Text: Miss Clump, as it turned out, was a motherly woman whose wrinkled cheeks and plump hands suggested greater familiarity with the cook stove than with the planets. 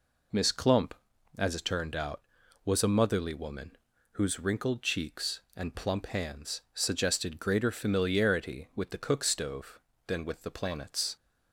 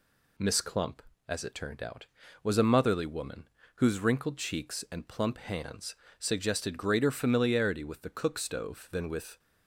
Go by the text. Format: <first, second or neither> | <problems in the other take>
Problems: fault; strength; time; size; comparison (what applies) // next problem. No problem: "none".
first | pauses between "woman" and "whose"; slight; at 3.4 s; 0.28 s long; slight in the first // pauses between "hands" and "suggested"; slight; at 5.9 s; 0.24 s long // stops before "the planets"; at 9.3 s